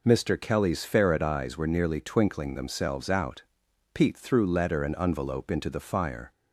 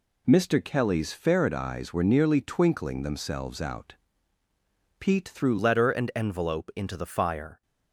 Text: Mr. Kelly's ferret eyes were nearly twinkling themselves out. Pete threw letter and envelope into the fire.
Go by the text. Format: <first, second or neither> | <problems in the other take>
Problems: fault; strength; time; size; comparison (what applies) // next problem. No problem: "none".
first | changes voice at "letter"; from 5.5 s on; 2.1 s long